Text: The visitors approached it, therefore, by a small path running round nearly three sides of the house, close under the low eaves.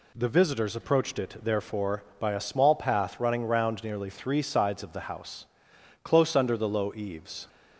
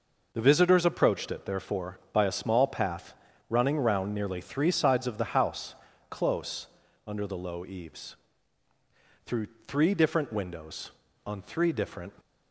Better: first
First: none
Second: pauses between "path" and "running"; slight; at 3.1 s; 0.34 s long // pauses between "close" and "under"; at 6.6 s; 0.40 s long // goes on to say "Through three different windows on three different"; strong; from 9.2 s on; 2.8 s long

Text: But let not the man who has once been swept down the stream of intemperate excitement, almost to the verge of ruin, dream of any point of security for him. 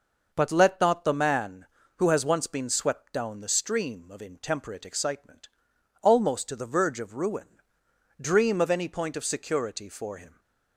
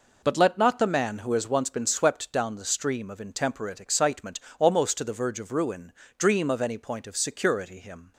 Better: first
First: none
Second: skips "for"; at 7.8 s

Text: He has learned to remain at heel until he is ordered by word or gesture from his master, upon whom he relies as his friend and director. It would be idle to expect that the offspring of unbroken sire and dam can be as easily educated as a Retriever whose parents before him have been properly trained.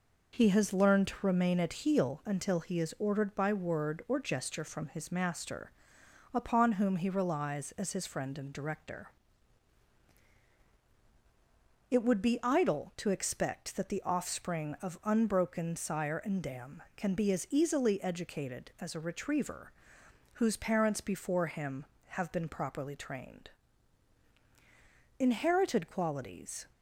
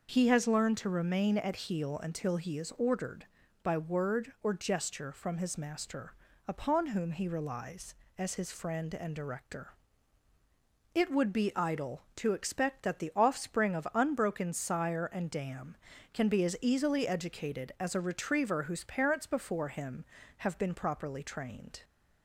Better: second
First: pauses between "Retriever" and "whose"; noticeable; at 19.6 s; 0.68 s long // goes on to say "Inherited qualities"; from 25.1 s on; 1.4 s long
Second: none

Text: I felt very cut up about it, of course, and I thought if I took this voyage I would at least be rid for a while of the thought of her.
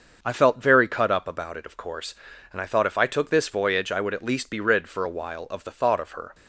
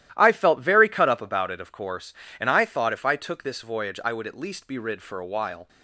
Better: first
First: starts louder than the rest; until 1.2 s; 6.5 dB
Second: starts louder than the rest; strong; until 1.1 s; 13.5 dB // stops before "of the thought of her"; at 5.6 s

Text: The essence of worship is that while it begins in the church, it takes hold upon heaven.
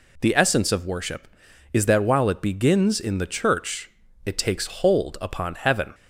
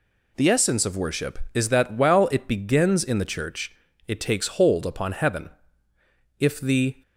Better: first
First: none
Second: goes on to say "If the"; noticeable; from 6.3 s on; 0.62 s long

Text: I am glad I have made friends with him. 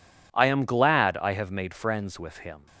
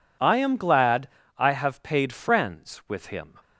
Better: first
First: none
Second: pauses between "glad" and "I"; slight; at 1.0 s; 0.28 s long // says "paid" for "made"; at 1.8 s

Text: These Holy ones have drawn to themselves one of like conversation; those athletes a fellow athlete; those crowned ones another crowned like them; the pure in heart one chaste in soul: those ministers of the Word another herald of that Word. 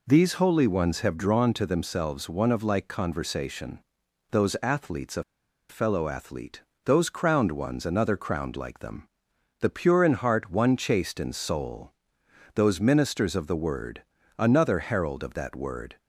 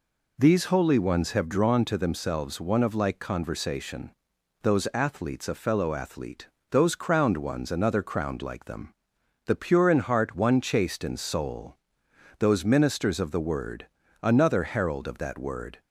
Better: second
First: pauses between "a" and "fellow"; noticeable; at 5.2 s; 0.47 s long // pauses between "Word" and "another"; slight; at 14.0 s; 0.34 s long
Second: pauses between "Word" and "another"; slight; at 13.8 s; 0.34 s long

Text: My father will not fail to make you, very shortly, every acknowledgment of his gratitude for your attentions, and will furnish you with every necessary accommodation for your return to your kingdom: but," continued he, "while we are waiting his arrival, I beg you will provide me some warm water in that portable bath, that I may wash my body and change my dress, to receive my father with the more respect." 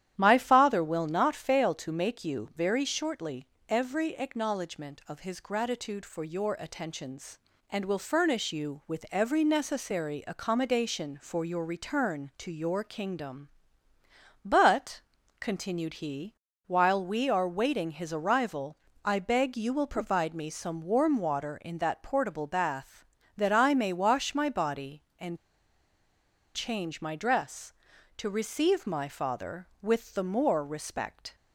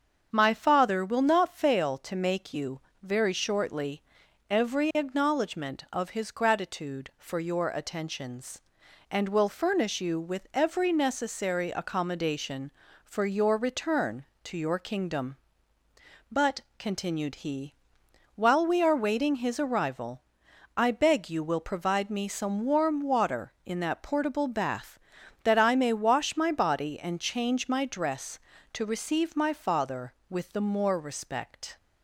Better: second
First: starts louder than the rest; strong; until 1.1 s; 11 dB // pauses between "and" and "change"; at 25.3 s; 1.1 s long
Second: starts louder than the rest; strong; until 1.3 s; 7 dB

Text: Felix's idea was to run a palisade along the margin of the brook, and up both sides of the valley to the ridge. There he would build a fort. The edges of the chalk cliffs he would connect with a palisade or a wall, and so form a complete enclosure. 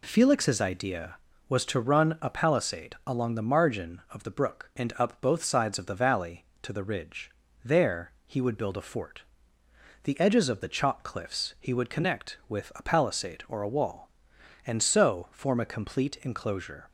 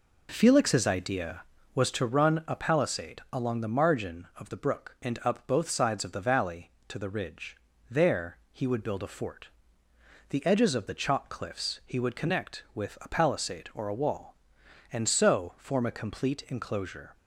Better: first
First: none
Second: starts louder than the rest; until 2.0 s; 4 dB

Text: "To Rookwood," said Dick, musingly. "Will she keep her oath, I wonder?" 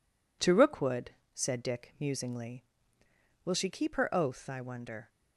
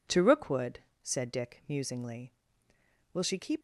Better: first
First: none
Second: stops before "her oath I wonder"; at 3.5 s

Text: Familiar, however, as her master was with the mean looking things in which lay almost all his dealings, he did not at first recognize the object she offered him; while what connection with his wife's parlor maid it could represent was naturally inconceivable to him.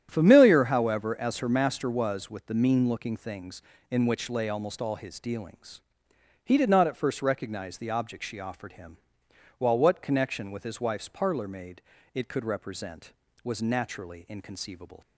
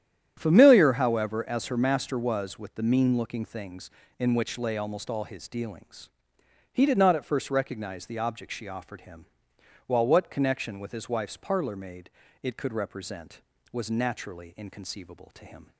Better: second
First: starts louder than the rest; strong; until 1.1 s; 10 dB // pauses between "maid" and "it"; slight; at 11.7 s; 0.32 s long // stops before "to him"; at 15.0 s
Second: starts louder than the rest; strong; until 1.3 s; 10 dB // pauses between "maid" and "it"; slight; at 12.0 s; 0.32 s long

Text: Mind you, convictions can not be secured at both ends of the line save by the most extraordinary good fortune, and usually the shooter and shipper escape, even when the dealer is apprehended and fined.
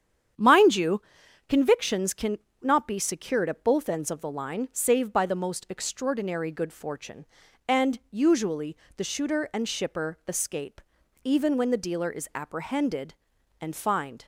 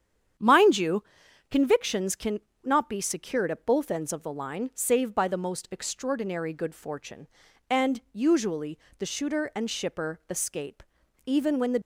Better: first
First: starts louder than the rest; strong; until 1.8 s; 9 dB // pauses between "can" and "not"; slight; at 2.3 s; 0.24 s long // pauses between "usually" and "the"; slight; at 8.7 s; 0.22 s long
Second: starts louder than the rest; strong; until 1.8 s; 9 dB // pauses between "can" and "not"; slight; at 2.3 s; 0.24 s long // pauses between "usually" and "the"; slight; at 8.7 s; 0.22 s long // stops before "dealer is apprehended and fined"; at 11.7 s

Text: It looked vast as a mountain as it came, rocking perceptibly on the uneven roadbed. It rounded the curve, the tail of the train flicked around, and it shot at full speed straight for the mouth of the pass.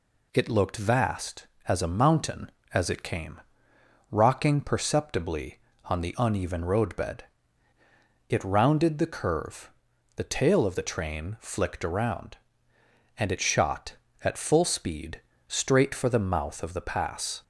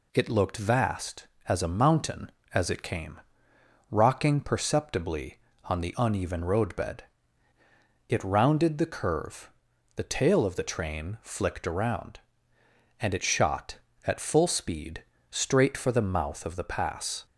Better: neither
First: pauses between "speed" and "straight"; slight; at 15.2 s; 0.26 s long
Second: pauses between "speed" and "straight"; slight; at 15.0 s; 0.26 s long

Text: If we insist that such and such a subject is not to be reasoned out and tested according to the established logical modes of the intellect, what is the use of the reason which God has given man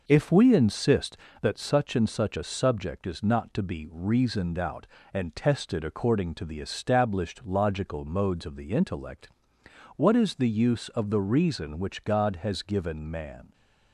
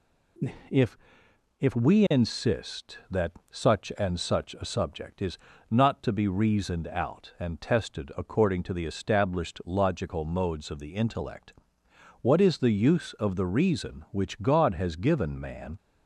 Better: first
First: none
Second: says "If" twice; at 1.5 s // pauses between "that" and "such"; slight; at 3.3 s; 0.18 s long // pauses between "is" and "not"; slight; at 5.3 s; 0.32 s long

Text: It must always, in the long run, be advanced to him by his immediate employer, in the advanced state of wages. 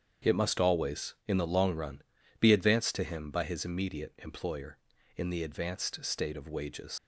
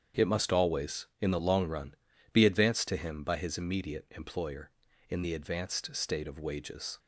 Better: second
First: starts louder than the rest; strong; until 1.3 s; 8 dB // leaves "wages" unfinished; at 6.9 s; 100 ms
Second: starts louder than the rest; strong; until 1.2 s; 8 dB

